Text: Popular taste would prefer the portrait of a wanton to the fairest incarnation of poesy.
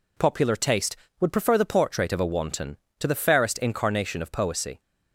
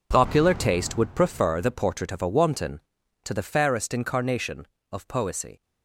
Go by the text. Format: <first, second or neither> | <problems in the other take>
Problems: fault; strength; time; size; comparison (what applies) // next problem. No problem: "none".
first | gets quieter; strong; throughout; 13.5 dB